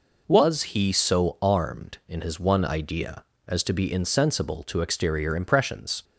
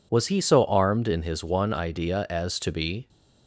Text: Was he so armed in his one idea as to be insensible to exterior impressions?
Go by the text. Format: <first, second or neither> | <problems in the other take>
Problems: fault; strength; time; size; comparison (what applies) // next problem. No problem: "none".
first | stops before "insensible to exterior impressions"; at 3.0 s